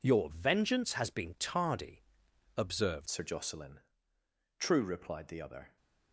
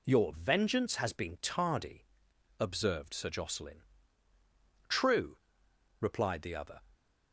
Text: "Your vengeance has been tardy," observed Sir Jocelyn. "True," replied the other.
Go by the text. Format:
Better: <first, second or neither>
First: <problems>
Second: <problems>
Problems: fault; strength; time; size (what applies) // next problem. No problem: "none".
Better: second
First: changes voice at "Sir"; from 3.0 s on; 2.7 s long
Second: none